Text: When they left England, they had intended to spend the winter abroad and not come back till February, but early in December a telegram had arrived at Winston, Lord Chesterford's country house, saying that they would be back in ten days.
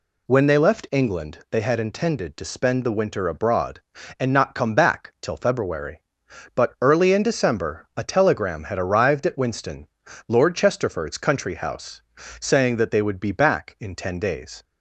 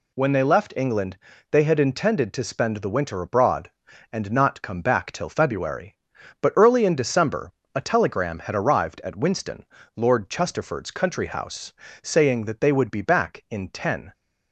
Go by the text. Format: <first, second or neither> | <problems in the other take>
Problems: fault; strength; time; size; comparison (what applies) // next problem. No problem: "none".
first | pauses between "December" and "a"; slight; at 7.5 s; 0.22 s long // stops before "days"; at 14.1 s